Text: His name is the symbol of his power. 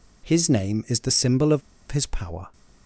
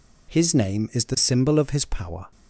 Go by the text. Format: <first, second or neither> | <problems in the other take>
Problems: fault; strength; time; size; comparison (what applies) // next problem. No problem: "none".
second | pauses between "of" and "his"; slight; at 1.6 s; 0.30 s long